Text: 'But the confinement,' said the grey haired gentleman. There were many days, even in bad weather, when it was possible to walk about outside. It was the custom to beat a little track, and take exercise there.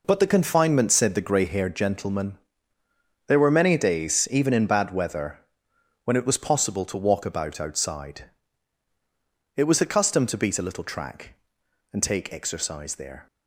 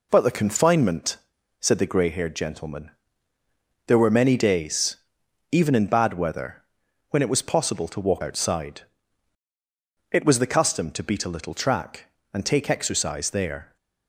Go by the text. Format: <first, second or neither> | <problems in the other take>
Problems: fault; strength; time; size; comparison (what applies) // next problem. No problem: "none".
first | skips "about"; at 8.2 s